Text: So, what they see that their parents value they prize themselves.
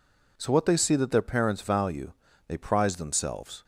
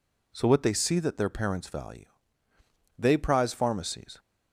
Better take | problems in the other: first | pauses between "value" and "they"; noticeable; at 2.0 s; 0.92 s long; slight in the first // says "pharmacies" for "themselves"; at 3.5 s

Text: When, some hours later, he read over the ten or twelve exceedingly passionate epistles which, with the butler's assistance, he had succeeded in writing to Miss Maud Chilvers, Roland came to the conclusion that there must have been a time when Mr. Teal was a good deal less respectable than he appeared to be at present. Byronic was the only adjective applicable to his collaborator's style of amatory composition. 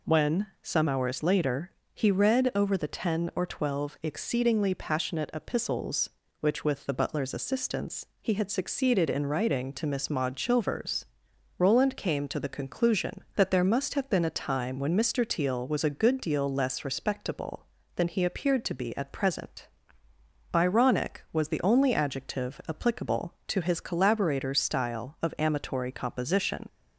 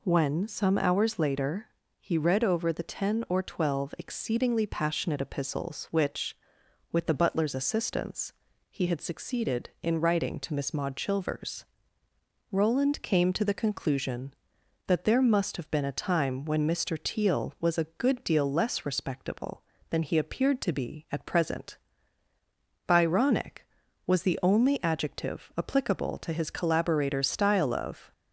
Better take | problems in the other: first | stops before "amatory composition"; at 28.1 s

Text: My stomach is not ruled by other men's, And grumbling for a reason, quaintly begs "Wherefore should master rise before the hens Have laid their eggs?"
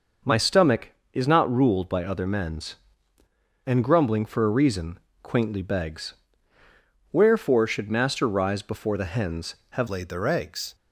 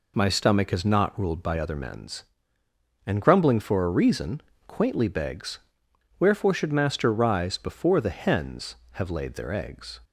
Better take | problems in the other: second | starts louder than the rest; noticeable; until 1.4 s; 6 dB // pauses between "begs" and "Wherefore"; noticeable; at 6.1 s; 0.96 s long; noticeable in the second // changes voice at "laid"; from 9.8 s on; 0.9 s long

